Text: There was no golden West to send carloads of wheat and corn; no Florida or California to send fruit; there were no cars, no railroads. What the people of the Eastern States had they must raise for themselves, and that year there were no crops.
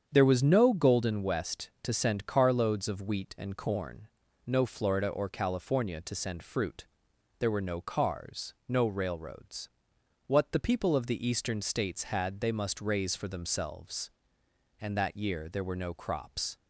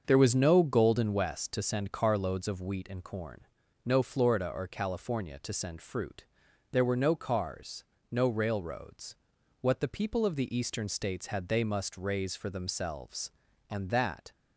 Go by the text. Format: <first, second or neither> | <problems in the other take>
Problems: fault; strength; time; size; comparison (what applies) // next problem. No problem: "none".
first | starts louder than the rest; until 1.0 s; 6.5 dB; strong in the first // stops before "year there were no crops"; at 14.3 s